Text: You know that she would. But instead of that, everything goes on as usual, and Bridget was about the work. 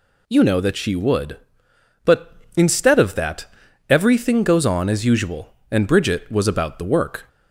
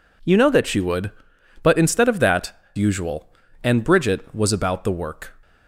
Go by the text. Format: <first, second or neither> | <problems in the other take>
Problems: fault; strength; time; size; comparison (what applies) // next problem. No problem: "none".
first | skips "everything goes on as"; at 2.6 s